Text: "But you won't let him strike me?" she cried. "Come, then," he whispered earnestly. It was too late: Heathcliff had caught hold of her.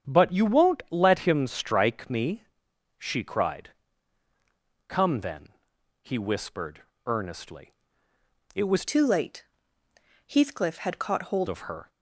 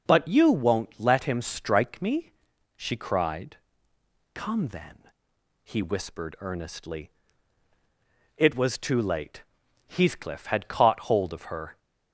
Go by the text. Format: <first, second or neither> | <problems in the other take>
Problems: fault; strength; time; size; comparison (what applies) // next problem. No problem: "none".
second | starts louder than the rest; strong; until 1.1 s; 8.5 dB // pauses between "whispered" and "earnestly"; slight; at 6.8 s; 0.24 s long // changes voice from "too" to "hold"; from 8.8 to 11.4 s; 2.6 s long